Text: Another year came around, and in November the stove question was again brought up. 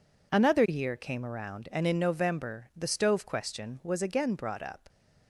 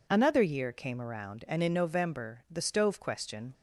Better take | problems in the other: first | stops before "was again brought up"; at 3.5 s

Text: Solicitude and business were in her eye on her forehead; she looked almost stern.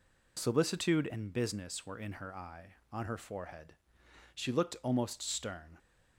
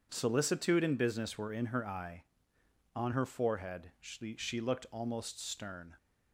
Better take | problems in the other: first | says "she" twice; at 4.3 s

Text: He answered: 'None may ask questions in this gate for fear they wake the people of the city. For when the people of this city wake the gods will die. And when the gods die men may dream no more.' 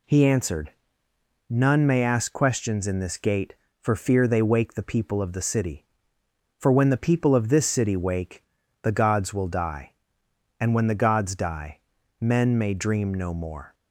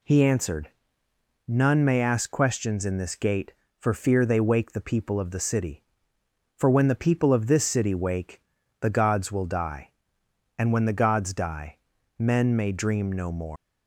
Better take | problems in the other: first | pauses between "wake" and "the"; at 8.3 s; 0.40 s long; also in the first // pauses between "die" and "men"; at 11.7 s; 0.40 s long; also in the first // leaves "more" unfinished; at 13.5 s; 160 ms

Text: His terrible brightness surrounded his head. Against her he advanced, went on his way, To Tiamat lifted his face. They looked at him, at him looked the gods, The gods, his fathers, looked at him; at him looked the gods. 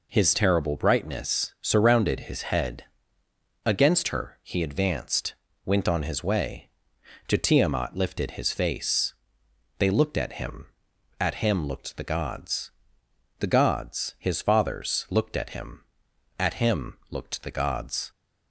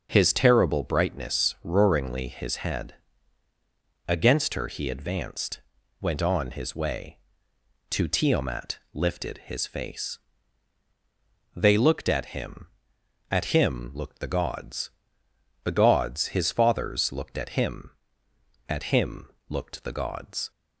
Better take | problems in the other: first | starts louder than the rest; until 1.1 s; 6 dB // says "roaringly" for "surrounded"; at 1.6 s // pauses between "him" and "looked"; slight; at 19.2 s; 0.20 s long

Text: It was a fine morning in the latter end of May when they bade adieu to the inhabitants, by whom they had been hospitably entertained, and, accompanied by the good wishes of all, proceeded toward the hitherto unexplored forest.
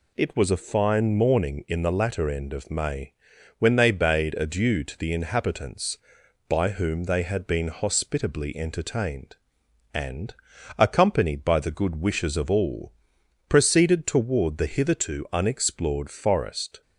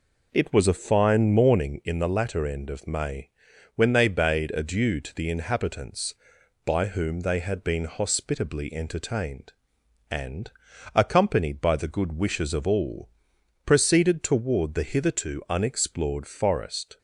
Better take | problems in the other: first | starts louder than the rest; noticeable; until 1.8 s; 4 dB // pauses between "May" and "when"; at 3.2 s; 0.44 s long; also in the first

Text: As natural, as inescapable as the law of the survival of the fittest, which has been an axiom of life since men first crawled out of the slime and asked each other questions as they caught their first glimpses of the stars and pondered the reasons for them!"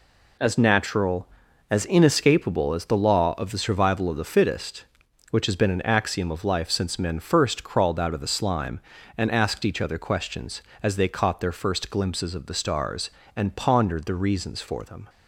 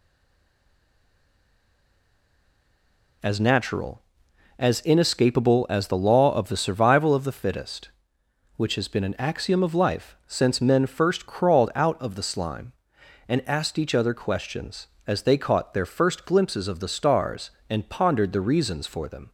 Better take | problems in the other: first | stays silent before the first word; strong; until 3.2 s; 3.2 s long

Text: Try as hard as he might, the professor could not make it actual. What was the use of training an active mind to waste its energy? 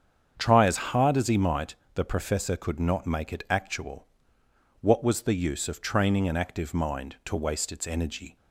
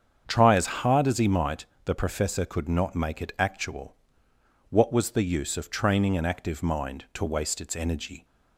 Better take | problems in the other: neither | starts louder than the rest; strong; the same in both

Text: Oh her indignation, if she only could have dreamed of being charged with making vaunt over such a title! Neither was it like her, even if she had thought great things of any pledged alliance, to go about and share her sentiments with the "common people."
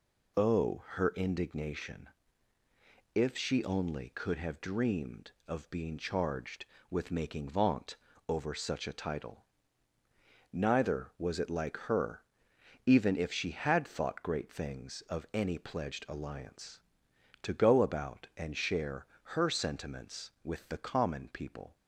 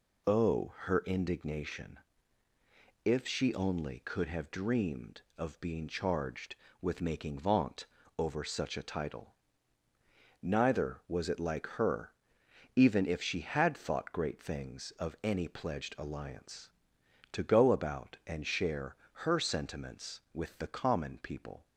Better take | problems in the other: neither | pauses between "vaunt" and "over"; slight; the same in both // pauses between "share" and "her"; slight; the same in both

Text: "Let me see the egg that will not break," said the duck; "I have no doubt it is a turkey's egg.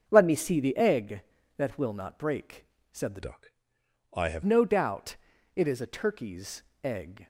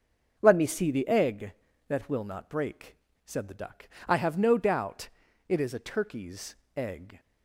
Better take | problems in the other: second | starts louder than the rest; until 1.0 s; 7 dB; also in the second // changes voice from "duck" to "have"; from 3.2 to 4.4 s; 1.2 s long // pauses between "doubt" and "it"; at 5.1 s; 0.40 s long; also in the second // pauses between "turkey's" and "egg"; slight; at 6.6 s; 0.22 s long; slight in the second

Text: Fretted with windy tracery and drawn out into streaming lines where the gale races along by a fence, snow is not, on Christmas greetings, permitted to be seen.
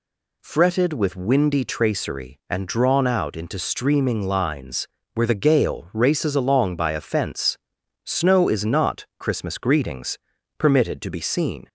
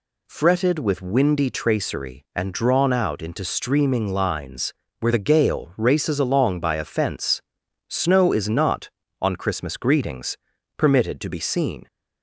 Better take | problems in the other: second | pauses between "lines" and "where"; slight; at 4.8 s; 0.26 s long; slight in the second // skips "on"; at 9.1 s

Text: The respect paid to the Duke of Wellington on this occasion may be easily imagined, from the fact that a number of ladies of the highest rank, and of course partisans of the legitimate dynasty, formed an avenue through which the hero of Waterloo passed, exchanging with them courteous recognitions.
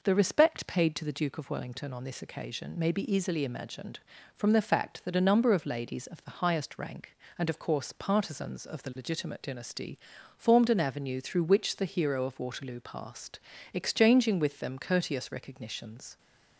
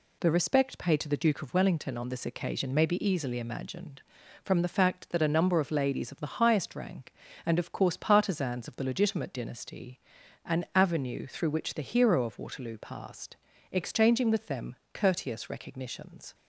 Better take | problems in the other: first | skips "formed"; at 10.2 s // pauses between "them" and "courteous"; slight; at 14.7 s; 0.18 s long

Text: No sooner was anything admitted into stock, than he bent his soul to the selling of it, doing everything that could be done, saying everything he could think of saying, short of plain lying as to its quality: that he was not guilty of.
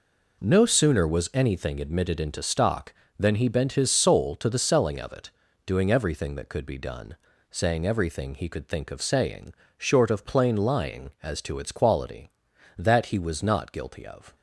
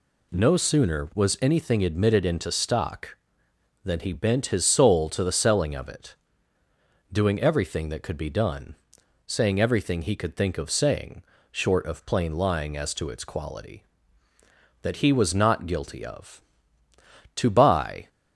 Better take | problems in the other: first | goes on to say "To buy"; noticeable; from 17.3 s on; 0.72 s long

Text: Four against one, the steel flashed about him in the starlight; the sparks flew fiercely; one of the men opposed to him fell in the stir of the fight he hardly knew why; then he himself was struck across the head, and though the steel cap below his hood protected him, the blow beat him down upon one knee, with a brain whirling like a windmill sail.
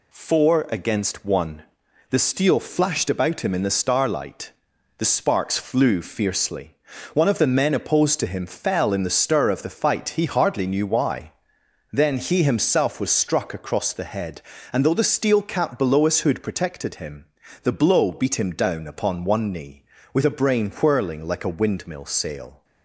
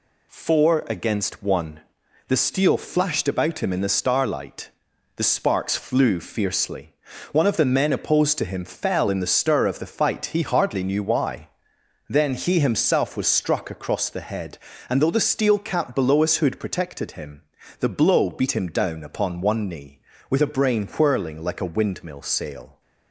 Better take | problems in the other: neither | none

